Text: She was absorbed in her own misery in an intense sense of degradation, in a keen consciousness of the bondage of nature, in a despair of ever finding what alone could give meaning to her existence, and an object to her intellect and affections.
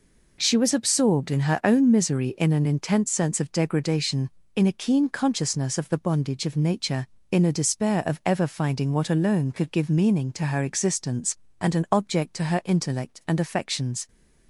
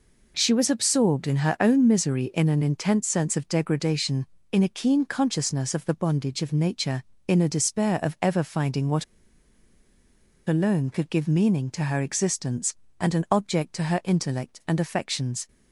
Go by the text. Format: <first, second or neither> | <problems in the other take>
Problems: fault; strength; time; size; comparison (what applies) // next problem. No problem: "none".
first | pauses between "what" and "alone"; strong; at 9.0 s; 1.4 s long